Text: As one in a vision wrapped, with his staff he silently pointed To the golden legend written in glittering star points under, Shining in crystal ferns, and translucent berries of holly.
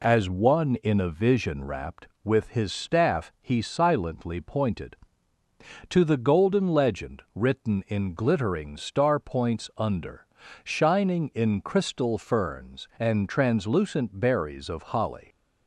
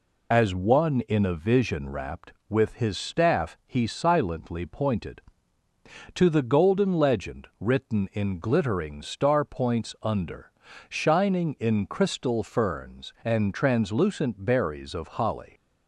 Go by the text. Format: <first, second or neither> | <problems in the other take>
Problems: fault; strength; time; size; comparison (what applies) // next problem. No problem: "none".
first | loses the start of "As"; at 0.3 s; 35 ms